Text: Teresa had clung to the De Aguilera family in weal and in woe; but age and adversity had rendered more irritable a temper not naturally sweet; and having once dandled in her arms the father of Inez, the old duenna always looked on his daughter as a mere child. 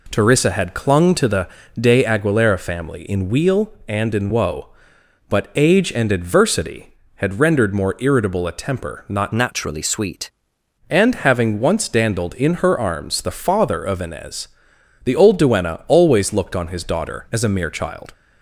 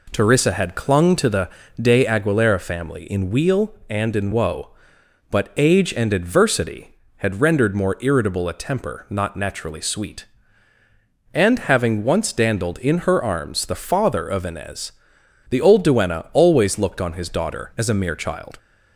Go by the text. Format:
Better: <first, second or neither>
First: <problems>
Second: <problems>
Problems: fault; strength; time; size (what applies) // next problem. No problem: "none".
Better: second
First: pauses between "the" and "De"; slight; at 1.4 s; 0.32 s long // changes voice from "naturally" to "sweet"; from 9.3 to 10.3 s; 1.0 s long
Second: pauses between "the" and "De"; slight; at 1.4 s; 0.32 s long